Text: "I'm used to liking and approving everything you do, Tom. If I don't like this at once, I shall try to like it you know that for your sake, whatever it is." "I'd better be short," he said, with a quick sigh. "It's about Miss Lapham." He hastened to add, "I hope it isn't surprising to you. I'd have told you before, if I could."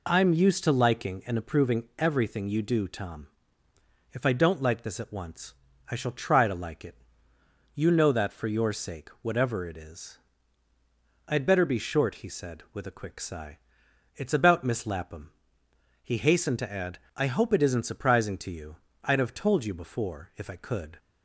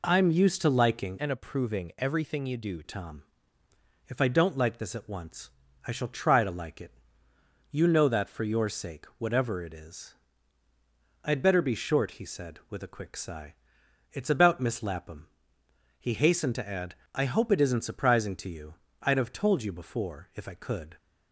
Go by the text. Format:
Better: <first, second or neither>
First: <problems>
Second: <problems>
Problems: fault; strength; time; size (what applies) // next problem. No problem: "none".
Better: first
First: pauses between "it" and "you"; noticeable; at 6.9 s; 0.82 s long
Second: changes voice from "and" to "do"; from 1.1 to 2.8 s; 1.7 s long // pauses between "it" and "you"; noticeable; at 6.9 s; 0.82 s long